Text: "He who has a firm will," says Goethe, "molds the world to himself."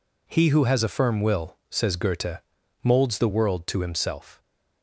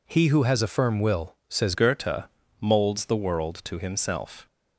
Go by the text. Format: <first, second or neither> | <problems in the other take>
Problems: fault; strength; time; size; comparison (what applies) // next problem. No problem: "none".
first | changes voice at "Goethe"; from 1.7 s on; 2.7 s long